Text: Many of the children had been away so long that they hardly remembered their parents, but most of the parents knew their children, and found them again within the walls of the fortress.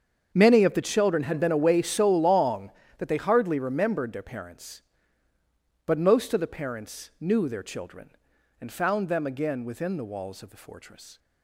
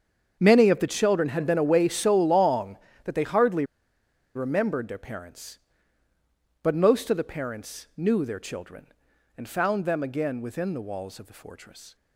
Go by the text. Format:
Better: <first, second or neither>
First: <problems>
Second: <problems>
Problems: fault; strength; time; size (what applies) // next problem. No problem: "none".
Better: first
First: starts louder than the rest; strong; until 1.3 s; 7.5 dB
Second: starts louder than the rest; strong; until 1.4 s; 7.5 dB // pauses between "hardly" and "remembered"; noticeable; at 3.6 s; 0.71 s long